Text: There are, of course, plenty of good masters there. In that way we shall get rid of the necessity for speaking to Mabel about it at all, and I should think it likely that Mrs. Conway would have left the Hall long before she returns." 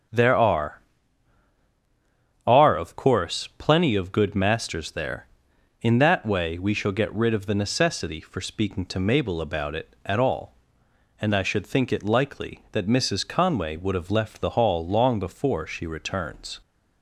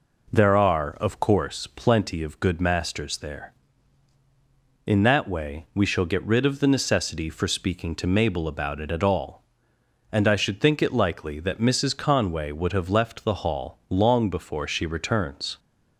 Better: second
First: starts louder than the rest; strong; until 2.7 s; 8 dB // says "are" twice; at 2.4 s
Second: none

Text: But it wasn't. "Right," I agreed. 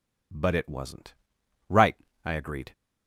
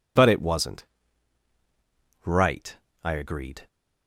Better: neither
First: none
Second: none

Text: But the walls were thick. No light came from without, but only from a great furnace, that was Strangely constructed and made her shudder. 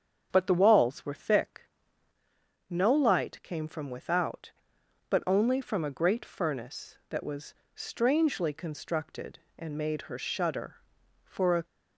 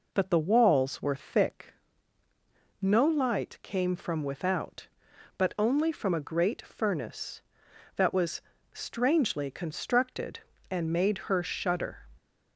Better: second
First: starts louder than the rest; strong; until 1.3 s; 7 dB // pauses between "was" and "Strangely"; slight; at 7.5 s; 0.22 s long // goes on to say "For a"; slight; from 11.2 s on; 0.40 s long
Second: pauses between "was" and "Strangely"; slight; at 8.4 s; 0.30 s long

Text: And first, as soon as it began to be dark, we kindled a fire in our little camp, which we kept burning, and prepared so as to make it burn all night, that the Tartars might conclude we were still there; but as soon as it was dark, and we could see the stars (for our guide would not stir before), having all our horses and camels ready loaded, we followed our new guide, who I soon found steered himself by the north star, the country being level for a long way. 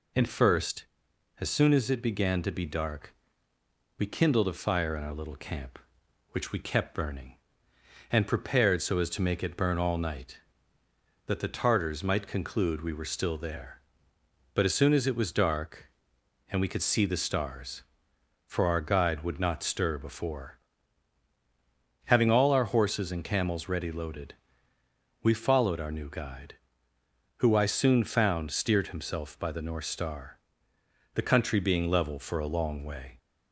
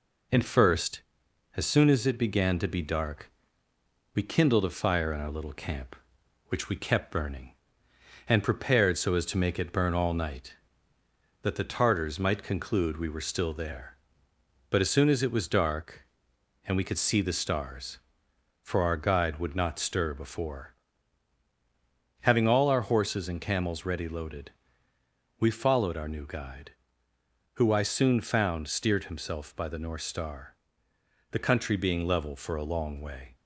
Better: first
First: none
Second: gets quieter; slight; throughout; 2 dB

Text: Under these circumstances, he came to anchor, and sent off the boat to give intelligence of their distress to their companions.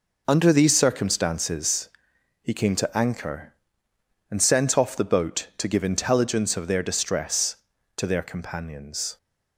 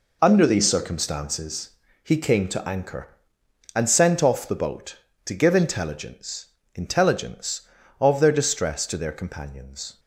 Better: first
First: none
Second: says "intelligence" twice; at 6.7 s

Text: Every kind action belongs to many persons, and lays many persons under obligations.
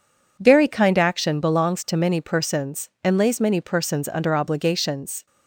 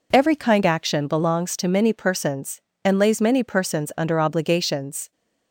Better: second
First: says "Very" for "Every"; at 0.3 s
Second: none

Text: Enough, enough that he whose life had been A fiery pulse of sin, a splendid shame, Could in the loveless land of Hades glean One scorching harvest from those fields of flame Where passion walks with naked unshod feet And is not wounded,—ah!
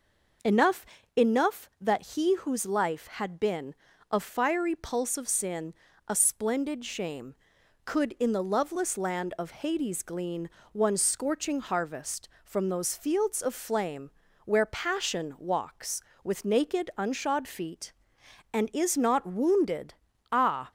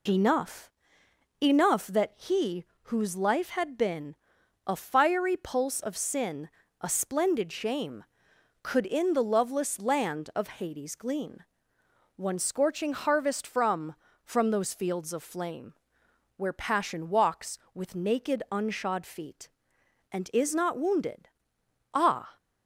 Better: first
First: pauses between "been" and "A"; slight; at 3.7 s; 0.36 s long // pauses between "glean" and "One"; slight; at 10.4 s; 0.24 s long // pauses between "flame" and "Where"; at 14.0 s; 0.38 s long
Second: pauses between "he" and "whose"; slight; at 2.6 s; 0.22 s long // pauses between "been" and "A"; noticeable; at 4.1 s; 0.50 s long // pauses between "glean" and "One"; noticeable; at 11.3 s; 0.76 s long // says "from" twice; at 14.2 s // pauses between "flame" and "Where"; noticeable; at 15.7 s; 0.64 s long

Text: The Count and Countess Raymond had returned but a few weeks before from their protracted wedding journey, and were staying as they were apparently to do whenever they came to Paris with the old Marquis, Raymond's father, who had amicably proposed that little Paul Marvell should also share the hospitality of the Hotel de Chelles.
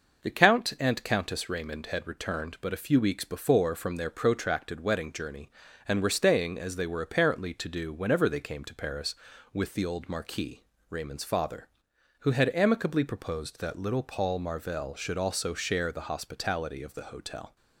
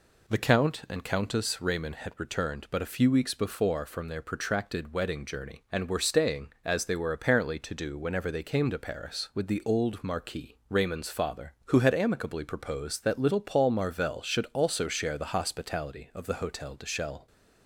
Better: second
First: stops before "de Chelles"; at 17.5 s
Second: none

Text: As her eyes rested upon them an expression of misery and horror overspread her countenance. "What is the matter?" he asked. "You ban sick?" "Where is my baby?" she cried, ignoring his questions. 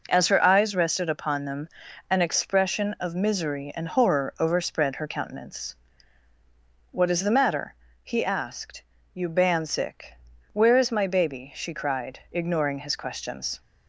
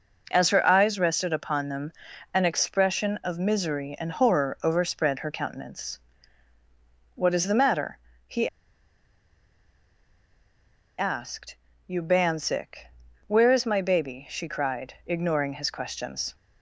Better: first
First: pauses between "them" and "an"; at 1.6 s; 0.42 s long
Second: pauses between "them" and "an"; at 1.9 s; 0.42 s long // pauses between "he" and "asked"; strong; at 8.4 s; 2.4 s long

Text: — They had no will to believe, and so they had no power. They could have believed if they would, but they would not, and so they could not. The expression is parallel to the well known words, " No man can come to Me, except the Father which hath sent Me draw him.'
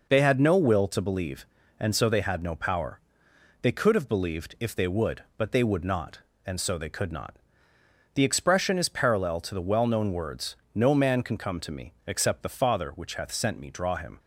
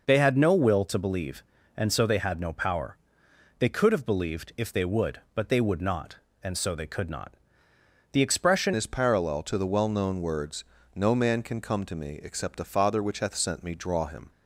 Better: first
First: none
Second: changes voice at "is"; from 8.7 s on; 5.6 s long

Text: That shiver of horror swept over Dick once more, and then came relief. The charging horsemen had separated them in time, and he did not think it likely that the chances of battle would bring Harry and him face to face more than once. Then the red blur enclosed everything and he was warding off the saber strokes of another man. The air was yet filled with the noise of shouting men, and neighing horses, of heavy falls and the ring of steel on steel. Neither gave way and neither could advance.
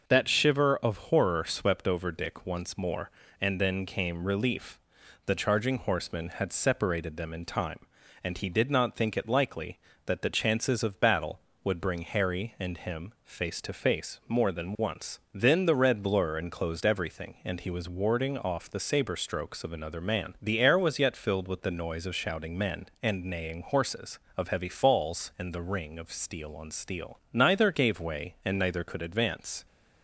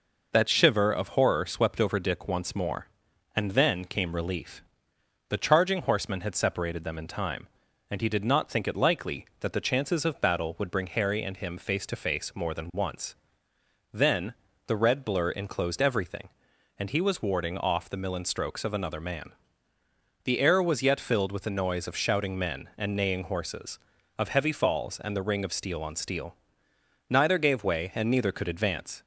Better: first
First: none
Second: pauses between "Then" and "the"; slight; at 14.3 s; 0.32 s long // says "millen" for "saber"; at 17.9 s

